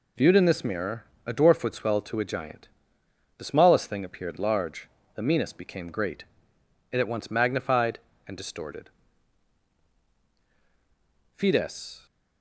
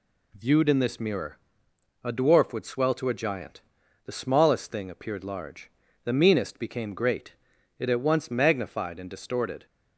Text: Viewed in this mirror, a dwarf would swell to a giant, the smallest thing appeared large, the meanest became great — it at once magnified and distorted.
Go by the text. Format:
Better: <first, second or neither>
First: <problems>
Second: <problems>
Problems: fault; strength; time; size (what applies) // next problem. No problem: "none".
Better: second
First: goes on to say "Fides"; noticeable; from 11.3 s on; 0.70 s long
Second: none